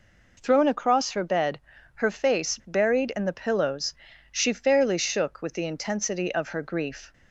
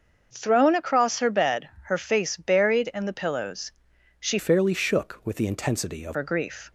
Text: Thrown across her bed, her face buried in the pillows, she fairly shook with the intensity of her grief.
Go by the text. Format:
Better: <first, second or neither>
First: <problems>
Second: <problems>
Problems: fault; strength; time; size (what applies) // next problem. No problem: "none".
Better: first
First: none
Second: starts louder than the rest; until 1.3 s; 6.5 dB // changes voice from "fairly" to "of"; from 4.3 to 6.1 s; 1.8 s long